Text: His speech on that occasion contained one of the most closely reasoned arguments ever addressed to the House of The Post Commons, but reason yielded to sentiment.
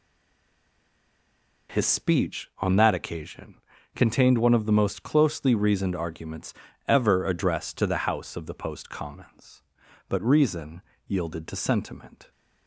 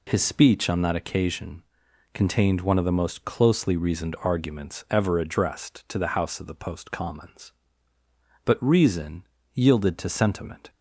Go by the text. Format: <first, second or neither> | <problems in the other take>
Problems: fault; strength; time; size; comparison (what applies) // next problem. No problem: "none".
second | stays silent before the first word; noticeable; until 1.6 s; 1.6 s long // pauses between "occasion" and "contained"; at 3.5 s; 0.40 s long; noticeable in the second // pauses between "arguments" and "ever"; slight; at 6.5 s; 0.36 s long // pauses between "reason" and "yielded"; slight; at 10.8 s; 0.26 s long; slight in the second